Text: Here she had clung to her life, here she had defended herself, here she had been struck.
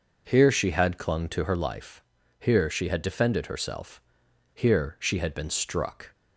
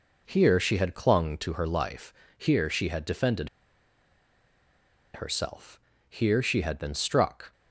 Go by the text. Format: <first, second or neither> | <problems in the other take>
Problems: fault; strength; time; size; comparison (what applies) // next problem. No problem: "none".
first | pauses between "defended" and "herself"; strong; at 3.4 s; 1.6 s long